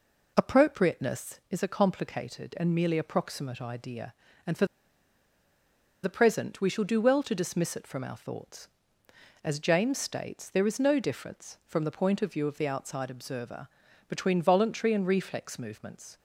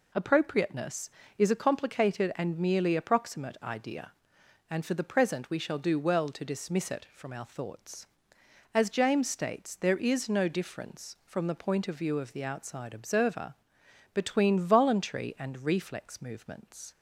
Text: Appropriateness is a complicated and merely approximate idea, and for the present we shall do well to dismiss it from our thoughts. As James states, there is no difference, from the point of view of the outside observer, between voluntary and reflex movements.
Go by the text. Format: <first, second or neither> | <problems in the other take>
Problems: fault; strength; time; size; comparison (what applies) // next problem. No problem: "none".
second | pauses between "for" and "the"; strong; at 4.6 s; 1.3 s long